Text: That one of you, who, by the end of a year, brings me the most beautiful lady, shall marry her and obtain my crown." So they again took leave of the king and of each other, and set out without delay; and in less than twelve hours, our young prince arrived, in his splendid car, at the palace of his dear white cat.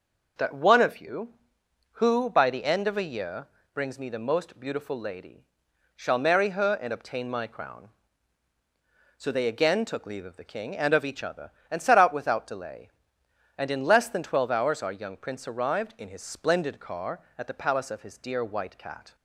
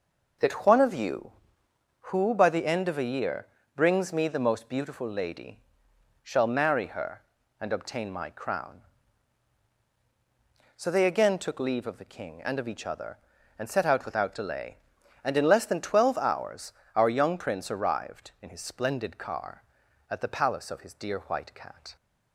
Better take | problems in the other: neither | none

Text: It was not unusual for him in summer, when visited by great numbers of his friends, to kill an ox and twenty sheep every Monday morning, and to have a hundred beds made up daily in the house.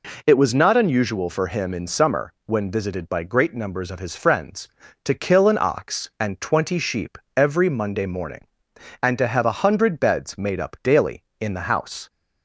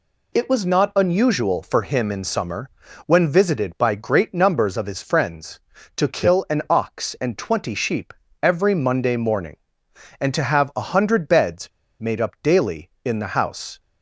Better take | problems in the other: first | pauses between "sheep" and "every"; slight; at 8.1 s; 0.30 s long; slight in the first // pauses between "beds" and "made"; slight; at 11.6 s; 0.31 s long

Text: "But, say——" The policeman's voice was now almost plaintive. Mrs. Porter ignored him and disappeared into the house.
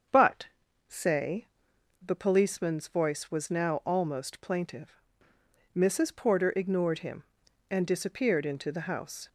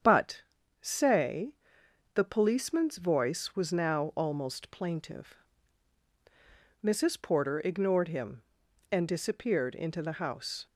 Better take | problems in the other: neither | starts louder than the rest; the same in both

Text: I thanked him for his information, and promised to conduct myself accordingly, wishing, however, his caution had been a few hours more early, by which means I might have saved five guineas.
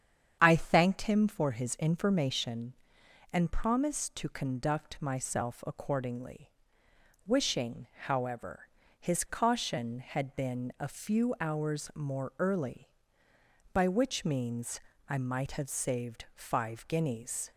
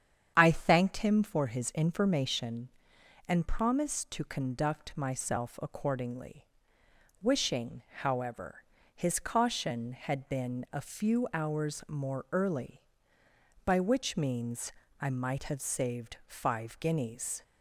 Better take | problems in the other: neither | starts louder than the rest; strong; the same in both // pauses between "means" and "I"; slight; the same in both

